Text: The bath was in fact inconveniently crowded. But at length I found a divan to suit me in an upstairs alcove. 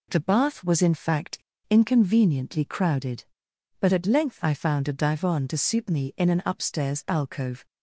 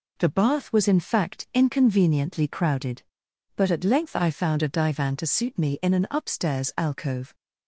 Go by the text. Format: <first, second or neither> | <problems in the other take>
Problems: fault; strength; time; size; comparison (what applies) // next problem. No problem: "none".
second | pauses between "fact" and "inconveniently"; slight; at 1.3 s; 0.31 s long